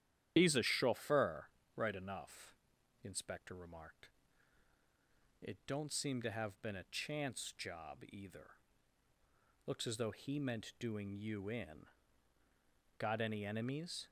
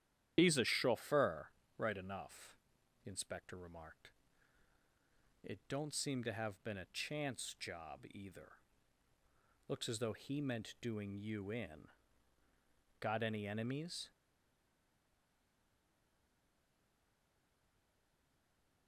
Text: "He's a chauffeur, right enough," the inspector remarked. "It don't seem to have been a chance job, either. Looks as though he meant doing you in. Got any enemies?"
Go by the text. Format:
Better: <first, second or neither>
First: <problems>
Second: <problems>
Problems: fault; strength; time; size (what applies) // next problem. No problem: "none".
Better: first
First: starts louder than the rest; strong; until 1.3 s; 11 dB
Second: starts louder than the rest; strong; until 1.3 s; 11 dB // stays silent after the last word; strong; from 14.1 s on; 4.7 s long